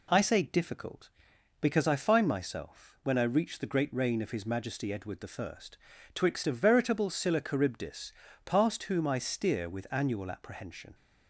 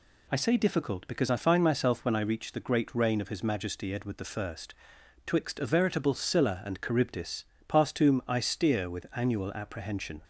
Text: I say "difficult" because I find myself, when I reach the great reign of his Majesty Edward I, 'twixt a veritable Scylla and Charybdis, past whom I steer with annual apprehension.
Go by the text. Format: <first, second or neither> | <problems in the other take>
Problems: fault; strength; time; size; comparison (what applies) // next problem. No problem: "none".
second | skips "and"; at 7.4 s